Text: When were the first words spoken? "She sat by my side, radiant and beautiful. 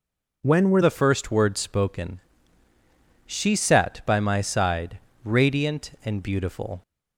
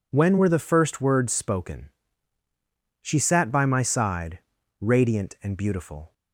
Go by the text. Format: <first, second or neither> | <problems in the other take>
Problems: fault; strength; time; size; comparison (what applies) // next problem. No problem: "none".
second | changes voice at "the"; from 0.8 s on; 6.0 s long